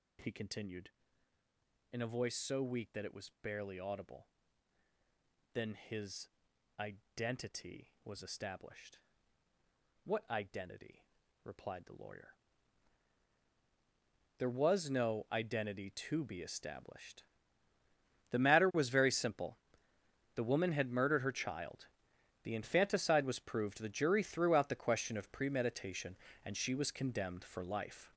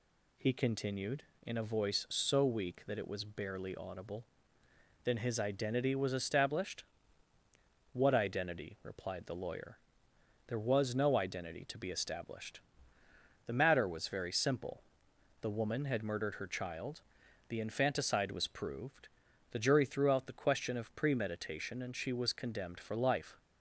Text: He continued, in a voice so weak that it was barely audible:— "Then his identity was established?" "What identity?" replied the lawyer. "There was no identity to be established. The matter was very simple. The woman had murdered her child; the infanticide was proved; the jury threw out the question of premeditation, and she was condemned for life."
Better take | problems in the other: second | gets louder; strong; throughout; 9 dB // pauses between "his" and "identity"; noticeable; at 6.2 s; 0.50 s long

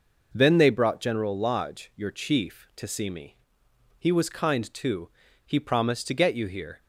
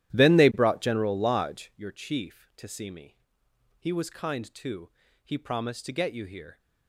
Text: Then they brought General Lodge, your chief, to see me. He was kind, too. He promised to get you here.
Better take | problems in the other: first | starts louder than the rest; strong; until 1.9 s; 12.5 dB

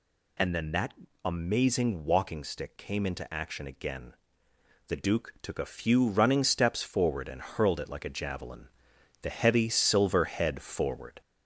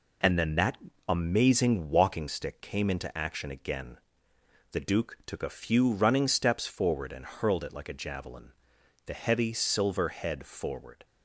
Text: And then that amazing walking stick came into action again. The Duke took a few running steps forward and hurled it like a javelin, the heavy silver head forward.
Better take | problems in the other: second | gets louder; slight; throughout; 2.5 dB // pauses between "that" and "amazing"; slight; at 0.9 s; 0.30 s long; slight in the second

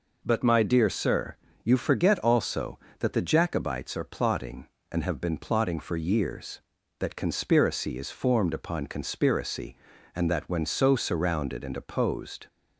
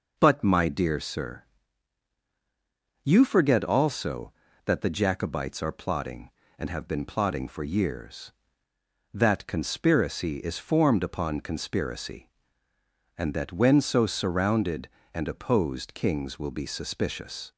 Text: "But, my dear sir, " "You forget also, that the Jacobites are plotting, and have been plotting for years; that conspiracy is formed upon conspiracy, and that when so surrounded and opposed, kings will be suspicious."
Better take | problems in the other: second | stops before "kings will be suspicious"; at 12.4 s

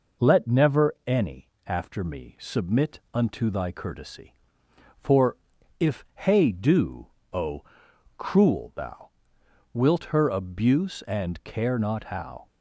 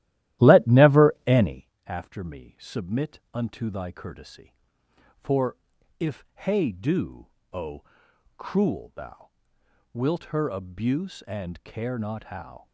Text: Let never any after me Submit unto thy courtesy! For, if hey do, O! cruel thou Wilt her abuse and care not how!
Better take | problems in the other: first | starts louder than the rest; strong; until 1.7 s; 14 dB // pauses between "any" and "after"; slight; at 1.6 s; 0.18 s long; slight in the first // pauses between "thou" and "Wilt"; noticeable; at 9.2 s; 0.64 s long; noticeable in the first

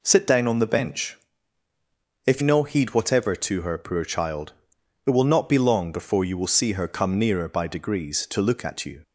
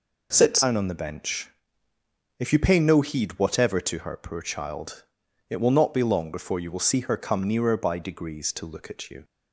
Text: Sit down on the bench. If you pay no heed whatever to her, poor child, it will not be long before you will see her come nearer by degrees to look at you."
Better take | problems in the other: second | skips "you pay"; at 2.4 s

